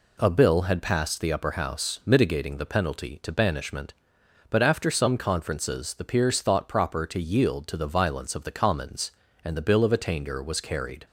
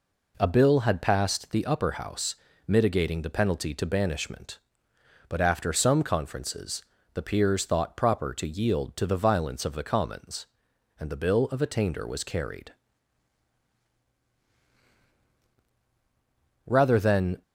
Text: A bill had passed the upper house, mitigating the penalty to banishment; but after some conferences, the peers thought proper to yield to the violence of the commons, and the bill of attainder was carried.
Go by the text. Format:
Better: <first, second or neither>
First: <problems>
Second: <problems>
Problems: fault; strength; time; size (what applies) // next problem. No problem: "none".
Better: first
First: none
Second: goes on to say "Rather than"; noticeable; from 16.6 s on; 0.76 s long